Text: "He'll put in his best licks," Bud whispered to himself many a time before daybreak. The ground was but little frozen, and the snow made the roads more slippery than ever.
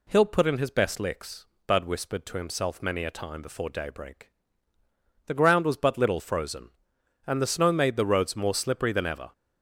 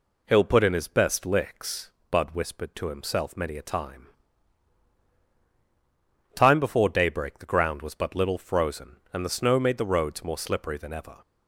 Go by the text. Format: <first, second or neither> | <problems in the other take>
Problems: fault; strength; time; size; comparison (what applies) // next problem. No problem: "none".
first | says "time" twice; at 6.3 s